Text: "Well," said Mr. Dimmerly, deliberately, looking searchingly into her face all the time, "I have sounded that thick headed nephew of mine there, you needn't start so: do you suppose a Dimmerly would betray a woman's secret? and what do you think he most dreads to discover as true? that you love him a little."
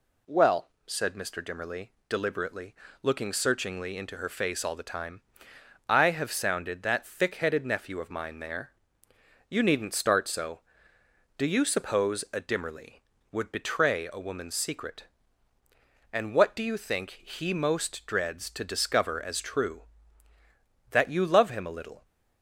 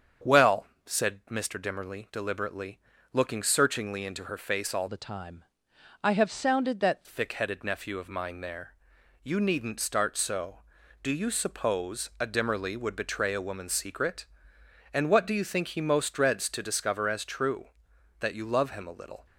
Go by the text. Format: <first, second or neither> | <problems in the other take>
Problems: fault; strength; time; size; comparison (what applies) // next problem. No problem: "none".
first | starts louder than the rest; strong; until 1.4 s; 7.5 dB // changes voice from "the" to "that"; from 4.8 to 7.0 s; 2.2 s long